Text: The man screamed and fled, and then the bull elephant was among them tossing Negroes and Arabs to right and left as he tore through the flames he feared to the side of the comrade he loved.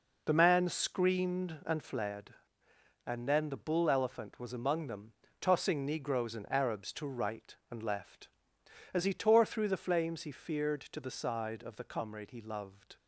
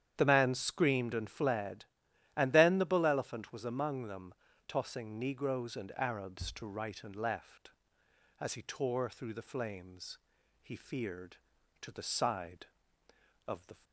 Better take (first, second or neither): first